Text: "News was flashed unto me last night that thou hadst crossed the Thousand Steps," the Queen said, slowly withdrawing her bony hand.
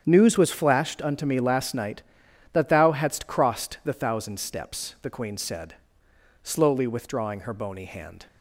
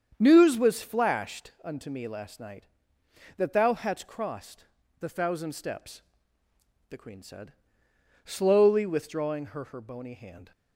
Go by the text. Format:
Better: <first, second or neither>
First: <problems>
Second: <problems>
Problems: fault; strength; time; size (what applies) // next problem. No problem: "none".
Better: first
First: starts louder than the rest; strong; until 1.0 s; 8.5 dB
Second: starts louder than the rest; strong; until 1.2 s; 8 dB // pauses between "crossed" and "the"; slight; at 4.6 s; 0.34 s long // says "her" twice; at 9.6 s